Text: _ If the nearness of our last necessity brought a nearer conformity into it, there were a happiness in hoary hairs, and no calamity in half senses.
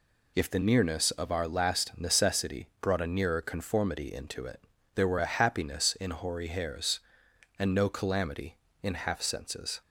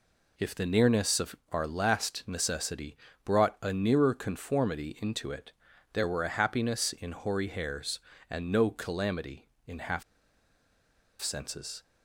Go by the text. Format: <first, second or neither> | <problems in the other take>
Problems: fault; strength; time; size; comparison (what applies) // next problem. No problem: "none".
first | pauses between "of" and "our"; slight; at 1.3 s; 0.16 s long // pauses between "necessity" and "brought"; slight; at 2.9 s; 0.28 s long // pauses between "half" and "senses"; at 10.0 s; 1.1 s long